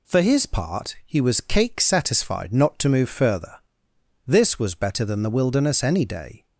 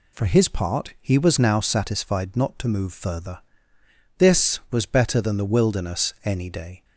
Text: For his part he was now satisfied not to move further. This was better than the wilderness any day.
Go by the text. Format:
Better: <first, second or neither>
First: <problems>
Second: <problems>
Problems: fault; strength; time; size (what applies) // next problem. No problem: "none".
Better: second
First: says "cake" for "now"; at 1.3 s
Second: none